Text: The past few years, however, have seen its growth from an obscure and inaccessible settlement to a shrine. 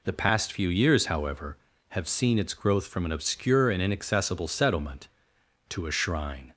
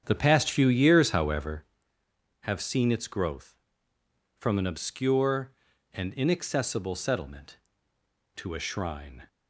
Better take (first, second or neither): first